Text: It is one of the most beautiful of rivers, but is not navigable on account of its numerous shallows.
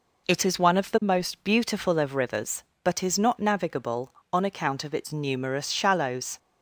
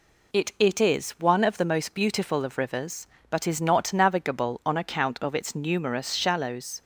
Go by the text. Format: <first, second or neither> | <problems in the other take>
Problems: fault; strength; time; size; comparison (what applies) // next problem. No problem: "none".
first | says "It" twice; at 0.5 s